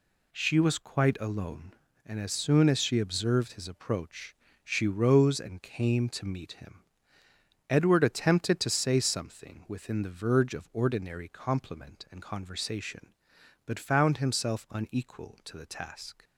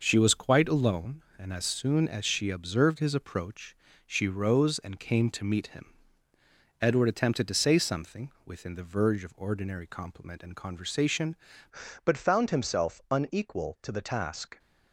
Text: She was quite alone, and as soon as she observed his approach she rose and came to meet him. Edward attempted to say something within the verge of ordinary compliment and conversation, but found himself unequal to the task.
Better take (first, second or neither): first